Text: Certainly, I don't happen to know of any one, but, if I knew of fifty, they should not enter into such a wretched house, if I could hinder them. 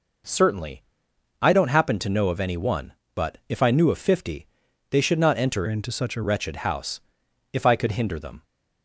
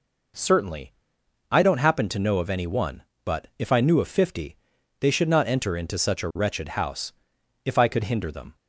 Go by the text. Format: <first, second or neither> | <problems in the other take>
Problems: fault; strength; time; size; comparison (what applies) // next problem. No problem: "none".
second | changes voice from "into" to "a"; from 5.6 to 6.2 s; 0.6 s long